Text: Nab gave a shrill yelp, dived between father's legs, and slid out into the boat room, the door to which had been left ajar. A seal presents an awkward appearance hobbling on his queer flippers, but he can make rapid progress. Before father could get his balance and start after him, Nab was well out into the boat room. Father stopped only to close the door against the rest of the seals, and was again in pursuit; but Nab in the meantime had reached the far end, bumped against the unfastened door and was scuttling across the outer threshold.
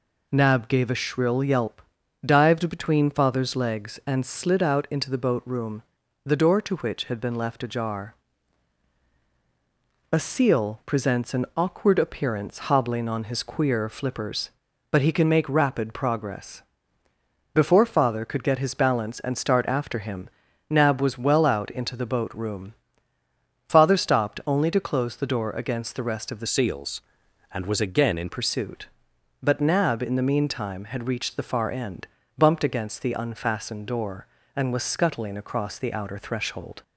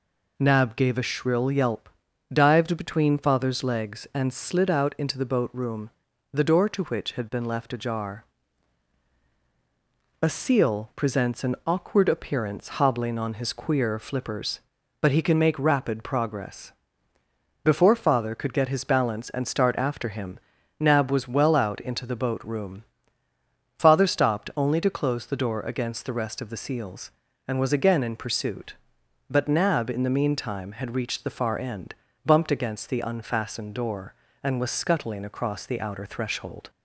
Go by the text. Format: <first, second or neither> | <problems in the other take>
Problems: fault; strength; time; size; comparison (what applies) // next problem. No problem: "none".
second | changes voice from "seals" to "in"; from 26.4 to 28.3 s; 1.9 s long